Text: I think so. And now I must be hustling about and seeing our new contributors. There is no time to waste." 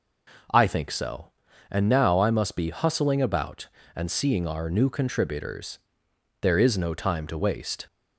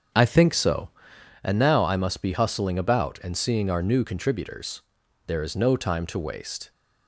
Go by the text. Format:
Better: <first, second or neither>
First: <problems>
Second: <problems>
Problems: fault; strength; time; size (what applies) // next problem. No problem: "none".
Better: first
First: none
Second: starts louder than the rest; strong; until 1.4 s; 7.5 dB